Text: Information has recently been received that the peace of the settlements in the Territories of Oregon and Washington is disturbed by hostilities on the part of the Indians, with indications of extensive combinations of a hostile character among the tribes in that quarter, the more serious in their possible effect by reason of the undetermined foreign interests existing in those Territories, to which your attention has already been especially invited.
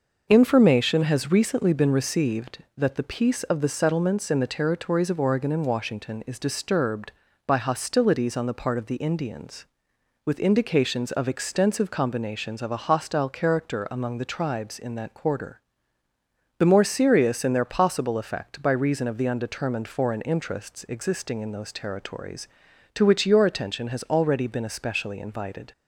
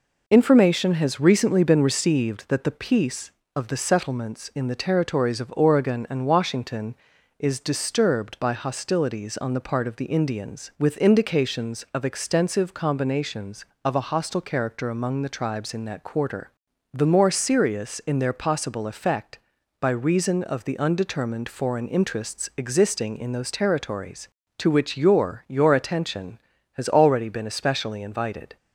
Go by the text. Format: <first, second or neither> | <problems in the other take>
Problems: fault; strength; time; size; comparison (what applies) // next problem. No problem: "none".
first | says "your" twice; at 25.4 s